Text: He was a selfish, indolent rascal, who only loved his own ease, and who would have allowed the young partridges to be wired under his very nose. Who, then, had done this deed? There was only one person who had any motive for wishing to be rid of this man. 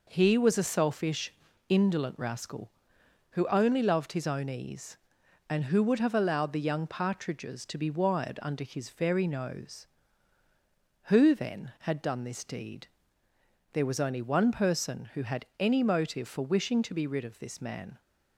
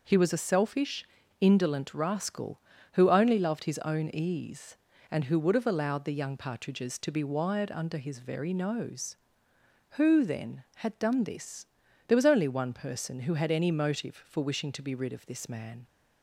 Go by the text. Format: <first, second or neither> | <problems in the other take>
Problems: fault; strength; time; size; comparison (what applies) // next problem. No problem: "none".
first | skips "deed"; at 11.8 s